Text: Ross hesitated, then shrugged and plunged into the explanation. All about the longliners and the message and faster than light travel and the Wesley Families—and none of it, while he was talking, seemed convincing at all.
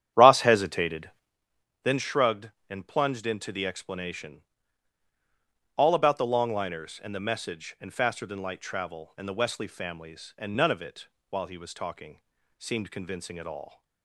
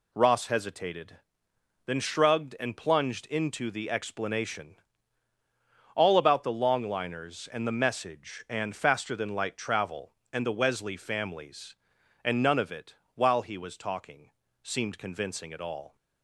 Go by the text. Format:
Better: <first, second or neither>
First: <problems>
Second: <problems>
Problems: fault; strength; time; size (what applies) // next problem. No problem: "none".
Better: second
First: starts louder than the rest; strong; until 1.4 s; 10.5 dB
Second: none